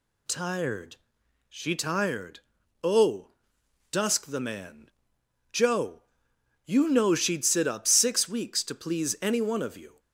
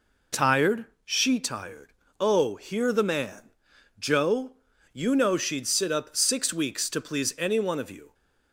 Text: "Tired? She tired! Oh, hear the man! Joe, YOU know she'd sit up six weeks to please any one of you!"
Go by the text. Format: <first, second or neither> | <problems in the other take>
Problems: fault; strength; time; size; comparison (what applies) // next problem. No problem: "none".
second | says "dusk" for "hear"; at 3.9 s